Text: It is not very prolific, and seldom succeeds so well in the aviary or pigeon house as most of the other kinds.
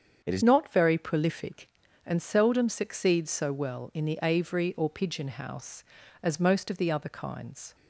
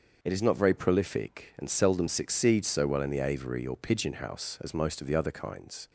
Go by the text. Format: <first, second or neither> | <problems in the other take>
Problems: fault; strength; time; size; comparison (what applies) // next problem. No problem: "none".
second | starts louder than the rest; strong; until 1.2 s; 7.5 dB; also in the second // changes voice at "not"; from 0.4 s on; 7.3 s long